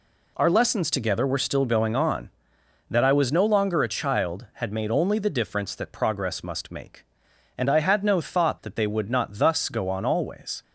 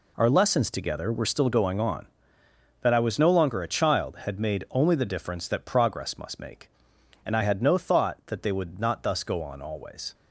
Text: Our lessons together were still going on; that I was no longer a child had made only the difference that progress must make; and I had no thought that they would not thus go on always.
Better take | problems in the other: neither | none

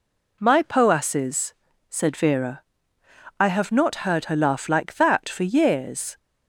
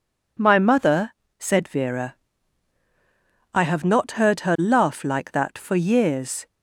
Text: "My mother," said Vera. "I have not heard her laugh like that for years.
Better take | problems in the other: second | says "poasses" for "mother"; at 0.6 s

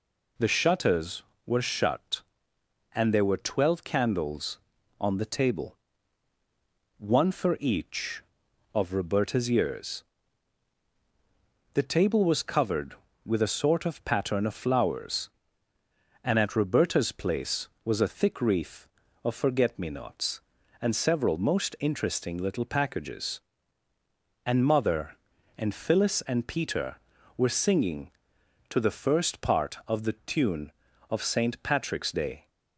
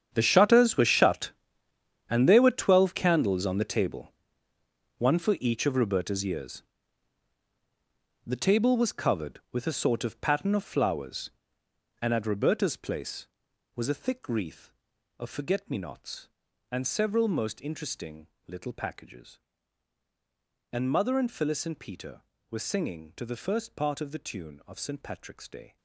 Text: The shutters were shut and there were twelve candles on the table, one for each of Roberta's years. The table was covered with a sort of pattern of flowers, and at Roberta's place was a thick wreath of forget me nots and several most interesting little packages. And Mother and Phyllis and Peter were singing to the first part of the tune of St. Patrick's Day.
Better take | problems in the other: first | gets quieter; strong; throughout; 16 dB // pauses between "interesting" and "little"; slight; at 18.2 s; 0.20 s long

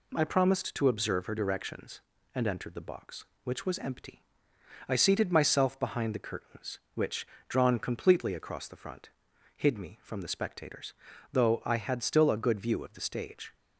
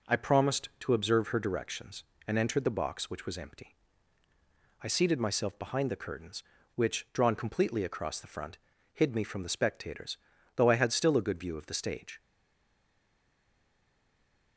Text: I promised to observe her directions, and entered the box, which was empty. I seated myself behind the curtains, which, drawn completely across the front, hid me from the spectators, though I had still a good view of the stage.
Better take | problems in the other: first | stays silent after the last word; from 12.2 s on; 2.3 s long

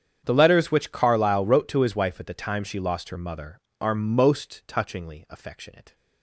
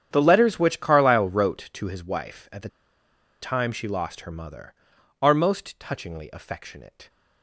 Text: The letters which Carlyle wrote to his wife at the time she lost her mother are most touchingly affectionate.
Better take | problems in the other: first | starts louder than the rest; strong; until 1.1 s; 9 dB; strong in the first // pauses between "the" and "time"; noticeable; at 2.6 s; 0.73 s long

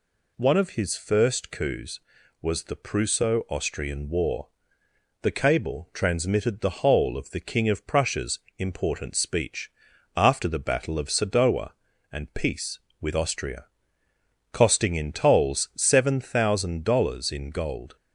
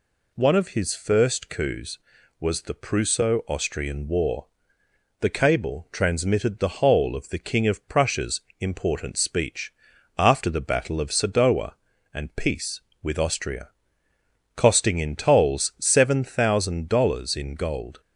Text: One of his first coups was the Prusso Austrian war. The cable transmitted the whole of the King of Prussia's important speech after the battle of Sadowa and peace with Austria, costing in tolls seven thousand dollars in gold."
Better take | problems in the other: neither | pauses between "Prussia's" and "important"; slight; the same in both // pauses between "speech" and "after"; noticeable; the same in both

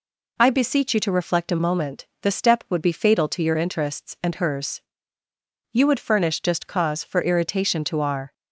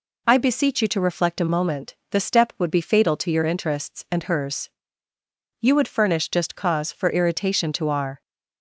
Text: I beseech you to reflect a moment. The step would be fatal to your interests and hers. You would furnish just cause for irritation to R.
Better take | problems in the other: neither | none

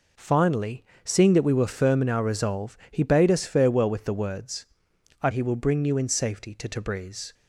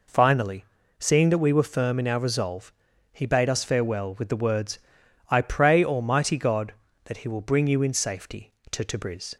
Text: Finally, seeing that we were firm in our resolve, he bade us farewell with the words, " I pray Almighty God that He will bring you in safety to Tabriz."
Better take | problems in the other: second | skips "pray Almighty God that"; at 5.3 s

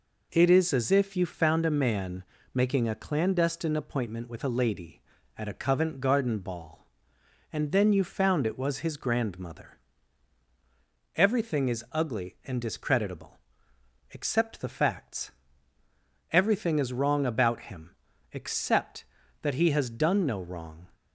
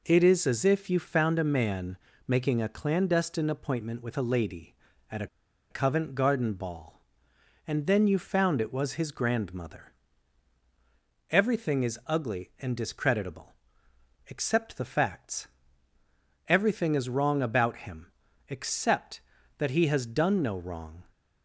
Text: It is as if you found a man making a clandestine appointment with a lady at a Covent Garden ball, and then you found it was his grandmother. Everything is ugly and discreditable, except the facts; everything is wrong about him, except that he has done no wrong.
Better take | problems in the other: first | pauses between "man" and "making"; slight; at 1.9 s; 0.30 s long; slight in the first // pauses between "a" and "Covent"; at 5.2 s; 0.43 s long

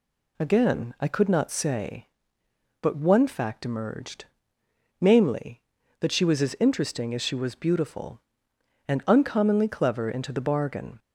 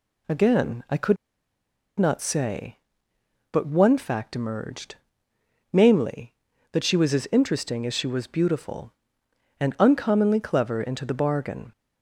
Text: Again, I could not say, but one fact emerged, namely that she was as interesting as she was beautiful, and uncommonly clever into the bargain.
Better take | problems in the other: first | pauses between "could" and "not"; noticeable; at 1.1 s; 0.83 s long

